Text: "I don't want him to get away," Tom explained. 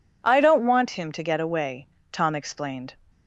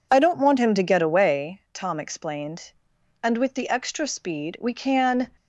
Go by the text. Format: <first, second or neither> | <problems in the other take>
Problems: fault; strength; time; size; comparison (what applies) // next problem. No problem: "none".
first | goes on to say "And with the extra speed we can"; strong; from 3.2 s on; 2.0 s long